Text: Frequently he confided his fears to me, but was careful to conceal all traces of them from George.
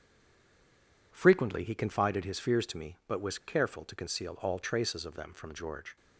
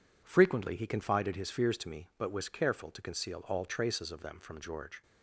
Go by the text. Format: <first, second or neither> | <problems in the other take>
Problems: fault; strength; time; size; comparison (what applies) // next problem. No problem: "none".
second | stays silent before the first word; until 1.1 s; 1.1 s long